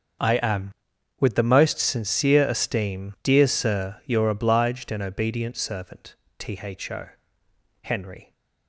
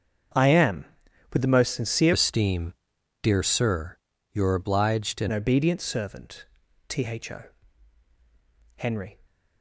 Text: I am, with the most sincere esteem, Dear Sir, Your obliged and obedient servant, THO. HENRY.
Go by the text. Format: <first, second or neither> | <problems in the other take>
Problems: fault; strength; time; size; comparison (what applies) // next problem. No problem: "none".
first | starts louder than the rest; until 1.8 s; 7 dB; also in the first // changes voice from "esteem" to "and"; from 2.1 to 5.2 s; 3.1 s long